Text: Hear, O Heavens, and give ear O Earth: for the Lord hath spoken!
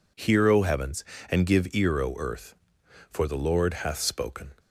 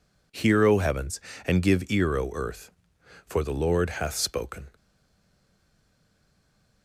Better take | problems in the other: first | stays silent after the last word; noticeable; from 4.7 s on; 2.1 s long

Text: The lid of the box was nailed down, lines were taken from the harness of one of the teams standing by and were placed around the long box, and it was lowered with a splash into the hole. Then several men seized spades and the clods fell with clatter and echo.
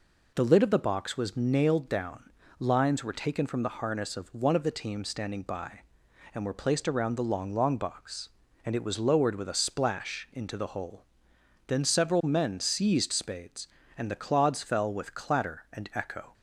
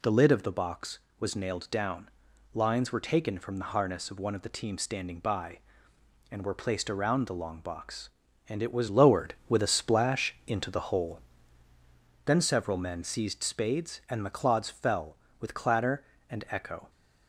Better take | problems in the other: second | says "long" twice; at 7.5 s

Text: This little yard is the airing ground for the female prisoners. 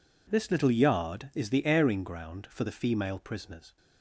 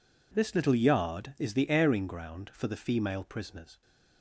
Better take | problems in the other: neither | none

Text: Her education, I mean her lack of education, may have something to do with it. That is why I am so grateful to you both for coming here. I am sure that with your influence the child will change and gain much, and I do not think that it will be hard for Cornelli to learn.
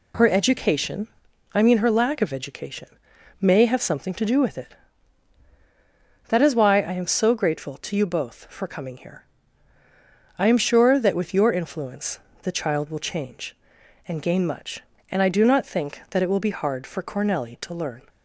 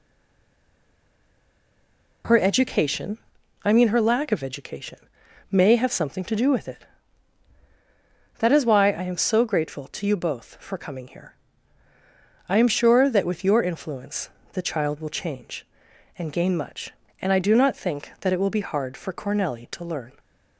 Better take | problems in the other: first | stays silent before the first word; until 2.2 s; 2.2 s long // pauses between "influence" and "the"; slight; at 14.2 s; 0.24 s long; slight in the first

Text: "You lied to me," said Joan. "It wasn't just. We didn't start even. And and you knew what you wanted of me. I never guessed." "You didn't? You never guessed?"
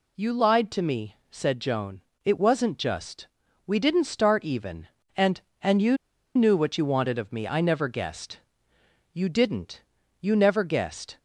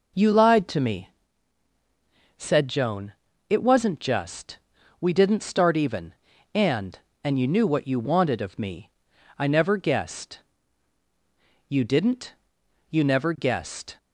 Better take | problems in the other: second | pauses between "you" and "knew"; at 5.9 s; 0.38 s long

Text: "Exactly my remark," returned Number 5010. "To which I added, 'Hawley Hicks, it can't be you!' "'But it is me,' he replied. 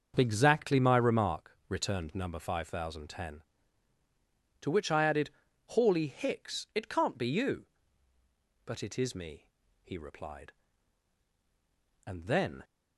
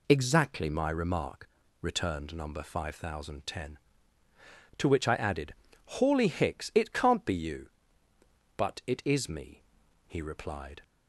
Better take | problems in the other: second | starts louder than the rest; until 1.1 s; 6.5 dB // goes on to say "And then"; from 12.0 s on; 0.56 s long

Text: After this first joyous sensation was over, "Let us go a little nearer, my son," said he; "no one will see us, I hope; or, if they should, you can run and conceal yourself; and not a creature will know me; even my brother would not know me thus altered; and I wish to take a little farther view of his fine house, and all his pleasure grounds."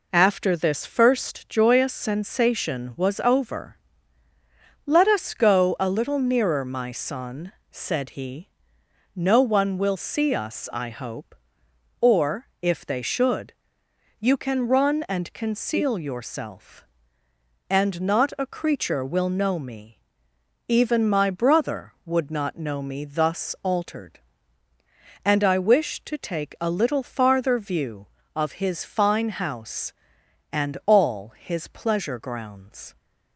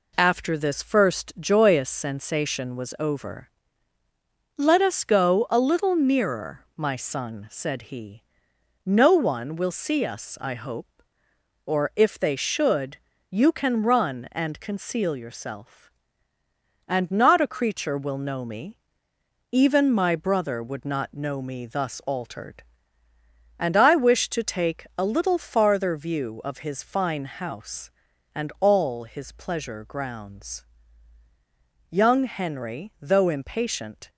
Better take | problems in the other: first | goes on to say "Young Henry though impatient"; strong; from 31.9 s on; 2.1 s long

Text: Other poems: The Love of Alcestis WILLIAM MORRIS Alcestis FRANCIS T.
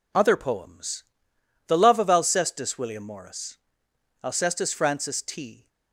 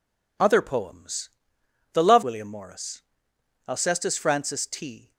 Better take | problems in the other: first | skips "of Alcestis"; at 2.2 s // pauses between "MORRIS" and "Alcestis"; noticeable; at 3.0 s; 0.66 s long; noticeable in the first

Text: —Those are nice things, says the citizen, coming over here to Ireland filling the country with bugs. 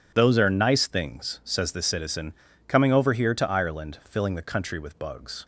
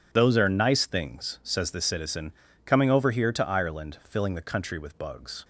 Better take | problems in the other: neither | none

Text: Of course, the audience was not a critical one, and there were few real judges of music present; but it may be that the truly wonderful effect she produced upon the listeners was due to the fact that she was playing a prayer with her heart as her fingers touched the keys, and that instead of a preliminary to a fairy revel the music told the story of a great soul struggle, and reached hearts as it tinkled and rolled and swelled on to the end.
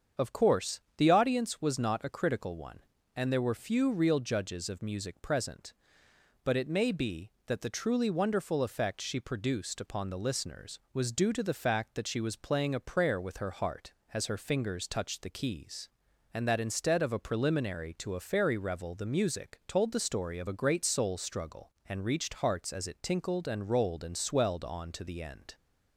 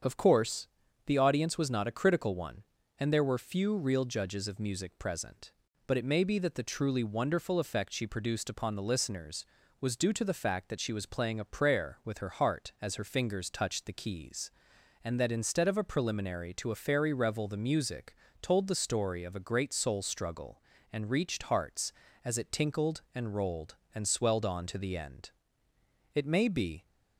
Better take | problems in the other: first | starts louder than the rest; until 1.4 s; 7 dB; strong in the first // pauses between "music" and "told"; slight; at 18.1 s; 0.28 s long // goes on to say "It may be"; noticeable; from 26.1 s on; 0.74 s long

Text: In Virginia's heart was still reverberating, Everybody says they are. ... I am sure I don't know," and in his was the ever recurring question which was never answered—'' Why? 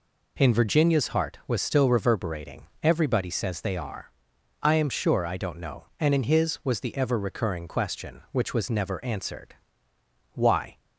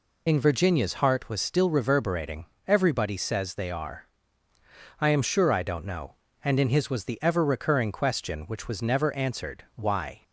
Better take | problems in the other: first | loses the start of "In"; at 0.2 s; 40 ms

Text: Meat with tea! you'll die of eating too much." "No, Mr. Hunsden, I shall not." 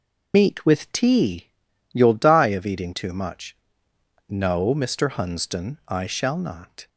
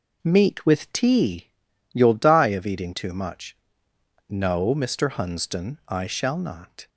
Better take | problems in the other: second | loses the start of "Meat"; at 0.3 s; 125 ms

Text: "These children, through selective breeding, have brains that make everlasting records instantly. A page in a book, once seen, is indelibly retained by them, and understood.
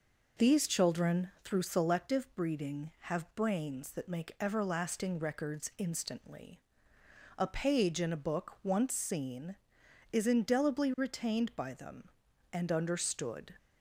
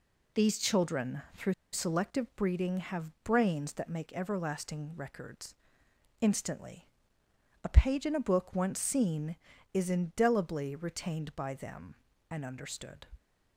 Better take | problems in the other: first | pauses between "through" and "selective"; slight; at 1.5 s; 0.18 s long // pauses between "records" and "instantly"; noticeable; at 5.5 s; 0.68 s long

